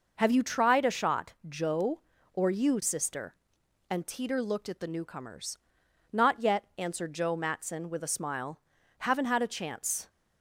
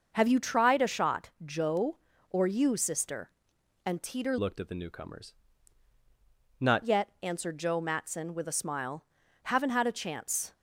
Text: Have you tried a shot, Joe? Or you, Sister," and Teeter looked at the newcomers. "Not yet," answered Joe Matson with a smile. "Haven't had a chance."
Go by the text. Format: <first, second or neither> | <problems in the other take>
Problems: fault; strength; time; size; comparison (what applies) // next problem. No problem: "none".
first | starts louder than the rest; noticeable; until 1.1 s; 6 dB // changes voice from "looked" to "Not"; from 4.3 to 6.8 s; 2.5 s long